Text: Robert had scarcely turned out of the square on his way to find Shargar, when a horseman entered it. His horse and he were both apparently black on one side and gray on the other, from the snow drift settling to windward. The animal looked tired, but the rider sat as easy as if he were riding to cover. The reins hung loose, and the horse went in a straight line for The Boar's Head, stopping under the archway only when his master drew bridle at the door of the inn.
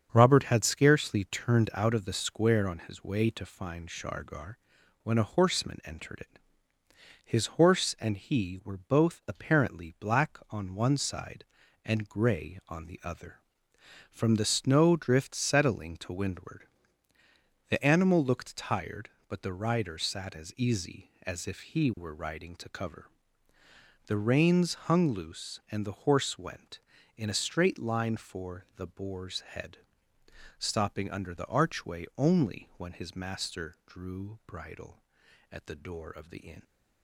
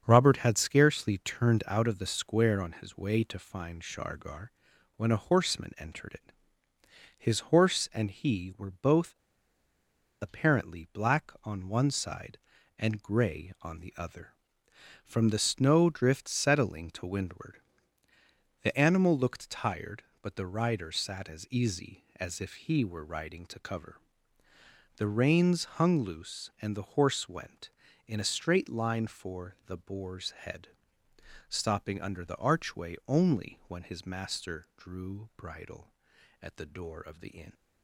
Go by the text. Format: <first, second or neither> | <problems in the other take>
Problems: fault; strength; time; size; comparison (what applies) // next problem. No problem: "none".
first | starts louder than the rest; strong; until 1.0 s; 7 dB; strong in the first // pauses between "both" and "apparently"; at 9.1 s; 1.0 s long